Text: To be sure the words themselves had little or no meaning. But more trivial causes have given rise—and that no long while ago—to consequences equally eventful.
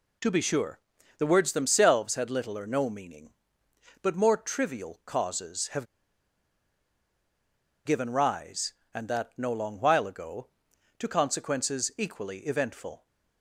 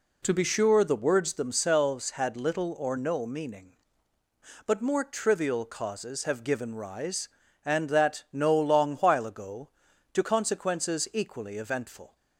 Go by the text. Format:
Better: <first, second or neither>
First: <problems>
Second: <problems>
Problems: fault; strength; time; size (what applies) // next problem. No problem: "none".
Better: second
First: pauses between "sure" and "the"; at 0.7 s; 0.40 s long // pauses between "have" and "given"; strong; at 5.8 s; 2.0 s long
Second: none